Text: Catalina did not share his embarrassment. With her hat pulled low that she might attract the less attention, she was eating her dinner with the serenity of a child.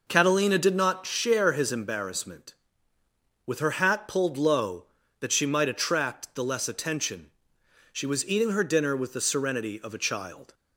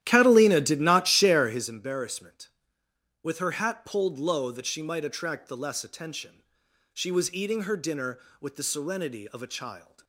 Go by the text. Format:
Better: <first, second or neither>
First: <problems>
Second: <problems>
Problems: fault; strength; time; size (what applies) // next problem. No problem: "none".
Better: first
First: none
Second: starts louder than the rest; strong; until 1.7 s; 12 dB